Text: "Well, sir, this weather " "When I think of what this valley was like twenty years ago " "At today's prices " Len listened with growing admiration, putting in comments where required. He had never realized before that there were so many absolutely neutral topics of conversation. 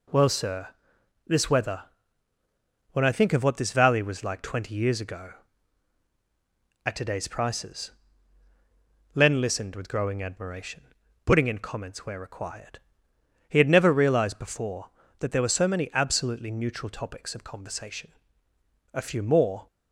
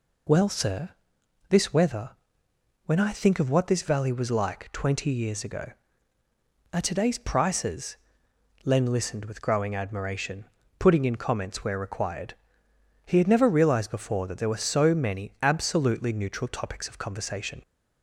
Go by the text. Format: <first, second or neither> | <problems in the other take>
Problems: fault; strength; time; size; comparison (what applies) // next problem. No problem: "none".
second | goes on to say "A few more"; noticeable; from 18.9 s on; 0.72 s long